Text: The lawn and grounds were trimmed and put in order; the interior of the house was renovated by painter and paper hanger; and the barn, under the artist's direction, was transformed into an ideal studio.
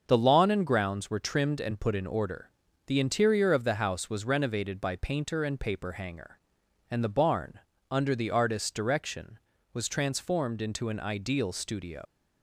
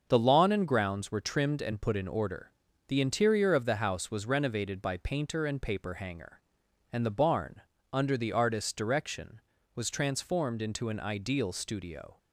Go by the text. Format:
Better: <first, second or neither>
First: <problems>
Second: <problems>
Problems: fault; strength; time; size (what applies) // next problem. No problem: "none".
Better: second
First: starts louder than the rest; until 1.0 s; 6.5 dB // leaves "studio" unfinished; at 12.0 s; 120 ms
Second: starts louder than the rest; until 1.1 s; 6.5 dB